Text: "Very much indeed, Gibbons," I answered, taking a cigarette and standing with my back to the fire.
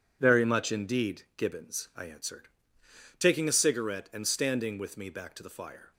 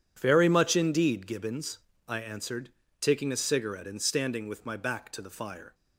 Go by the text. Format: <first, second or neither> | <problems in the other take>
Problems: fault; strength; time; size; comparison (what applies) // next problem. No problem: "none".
second | says "me" for "my"; at 4.9 s